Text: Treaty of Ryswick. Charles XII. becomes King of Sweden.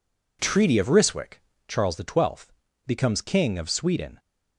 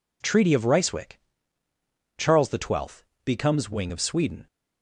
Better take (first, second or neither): first